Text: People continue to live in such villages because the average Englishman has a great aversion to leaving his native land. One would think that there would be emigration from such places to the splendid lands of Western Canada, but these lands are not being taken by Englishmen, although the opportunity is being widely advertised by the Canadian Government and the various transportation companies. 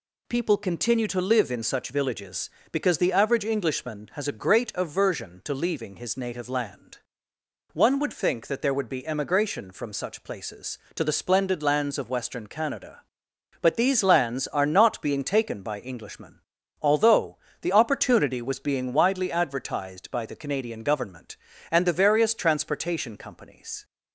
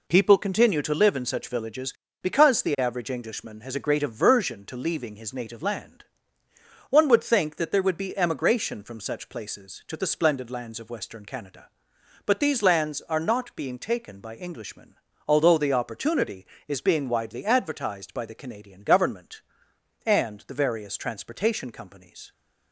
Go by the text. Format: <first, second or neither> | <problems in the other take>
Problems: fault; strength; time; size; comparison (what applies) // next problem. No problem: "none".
second | pauses between "although" and "the"; slight; at 17.3 s; 0.24 s long // says "was" for "is"; at 18.4 s